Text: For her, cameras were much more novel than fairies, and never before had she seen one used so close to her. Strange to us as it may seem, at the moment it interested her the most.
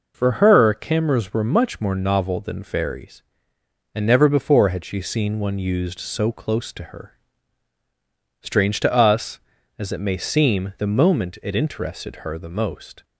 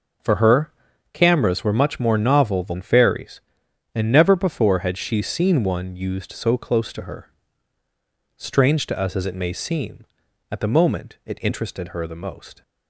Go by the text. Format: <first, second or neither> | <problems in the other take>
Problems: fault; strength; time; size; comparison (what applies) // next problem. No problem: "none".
second | skips "at"; at 10.7 s